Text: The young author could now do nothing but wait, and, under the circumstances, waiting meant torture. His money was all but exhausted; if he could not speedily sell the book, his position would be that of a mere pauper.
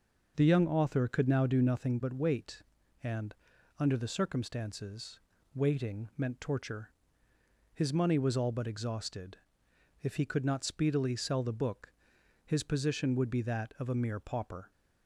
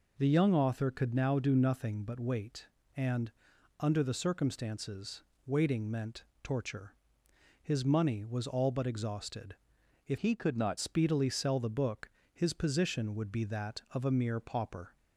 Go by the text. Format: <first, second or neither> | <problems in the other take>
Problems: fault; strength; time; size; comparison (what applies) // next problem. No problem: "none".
first | pauses between "meant" and "torture"; slight; at 6.2 s; 0.20 s long // changes voice from "he" to "not"; from 10.1 to 10.7 s; 0.6 s long